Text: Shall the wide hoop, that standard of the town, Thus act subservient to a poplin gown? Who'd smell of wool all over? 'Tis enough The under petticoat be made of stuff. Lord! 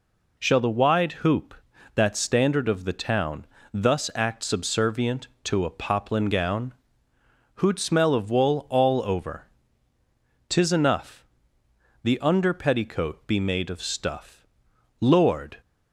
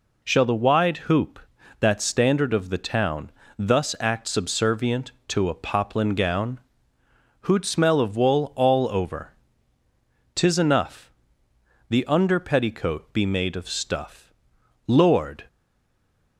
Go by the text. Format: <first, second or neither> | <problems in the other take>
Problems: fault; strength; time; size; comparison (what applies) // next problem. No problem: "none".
first | pauses between "enough" and "The"; noticeable; at 11.1 s; 0.78 s long; noticeable in the first // stays silent after the last word; slight; from 15.4 s on; 0.9 s long